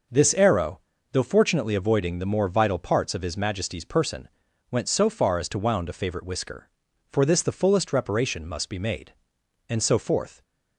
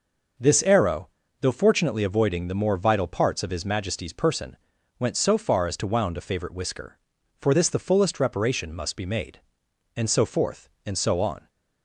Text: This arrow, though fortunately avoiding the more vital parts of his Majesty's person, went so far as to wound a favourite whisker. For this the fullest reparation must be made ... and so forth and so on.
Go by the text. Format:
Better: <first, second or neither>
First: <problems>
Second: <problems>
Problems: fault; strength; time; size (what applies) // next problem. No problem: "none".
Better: second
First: stops before "and so on"; at 10.4 s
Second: none